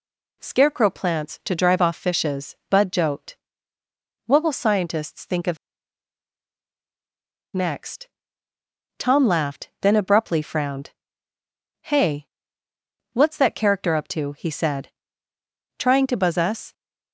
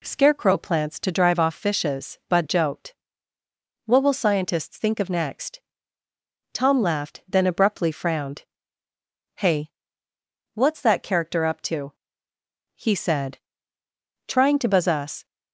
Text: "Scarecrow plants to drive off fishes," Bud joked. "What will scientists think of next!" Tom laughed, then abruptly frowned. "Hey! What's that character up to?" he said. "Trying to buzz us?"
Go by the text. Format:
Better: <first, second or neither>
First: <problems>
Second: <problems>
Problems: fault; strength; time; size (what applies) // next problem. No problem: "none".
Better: second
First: pauses between "of" and "next"; strong; at 5.5 s; 1.9 s long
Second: none